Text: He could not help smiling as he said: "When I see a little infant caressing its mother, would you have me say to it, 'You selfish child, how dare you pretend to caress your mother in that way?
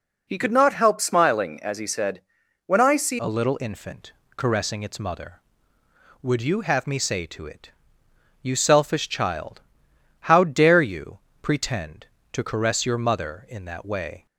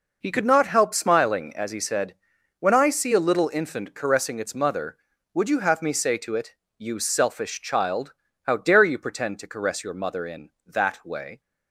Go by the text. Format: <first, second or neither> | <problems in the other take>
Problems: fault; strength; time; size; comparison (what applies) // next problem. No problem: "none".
second | changes voice at "a"; from 3.1 s on; 11.1 s long // pauses between "infant" and "caressing"; slight; at 4.1 s; 0.22 s long // pauses between "you" and "pretend"; slight; at 11.1 s; 0.24 s long